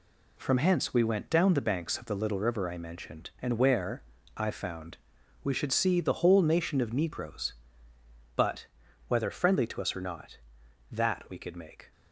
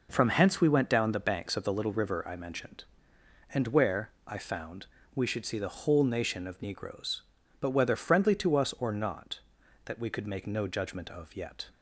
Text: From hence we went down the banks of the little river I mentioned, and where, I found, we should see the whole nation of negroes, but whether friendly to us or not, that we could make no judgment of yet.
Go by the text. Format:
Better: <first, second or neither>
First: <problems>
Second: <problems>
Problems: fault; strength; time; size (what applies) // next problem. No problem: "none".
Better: second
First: pauses between "but" and "whether"; at 8.6 s; 0.40 s long // stops before "no judgment of yet"; at 11.9 s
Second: none